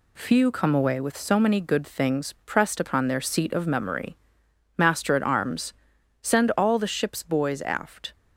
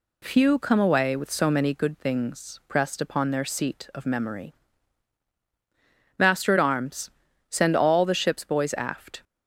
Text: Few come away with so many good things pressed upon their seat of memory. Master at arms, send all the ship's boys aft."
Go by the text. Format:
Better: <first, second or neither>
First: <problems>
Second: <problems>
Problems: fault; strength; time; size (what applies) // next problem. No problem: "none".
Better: second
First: gets quieter; noticeable; throughout; 5 dB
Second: none